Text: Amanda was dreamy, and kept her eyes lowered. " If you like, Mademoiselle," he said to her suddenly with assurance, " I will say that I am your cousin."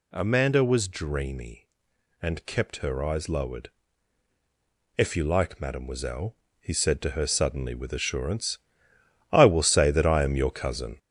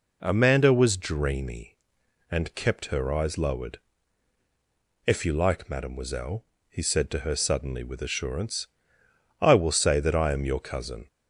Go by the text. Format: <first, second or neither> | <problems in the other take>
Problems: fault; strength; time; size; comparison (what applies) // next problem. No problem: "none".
second | gets louder; noticeable; throughout; 4.5 dB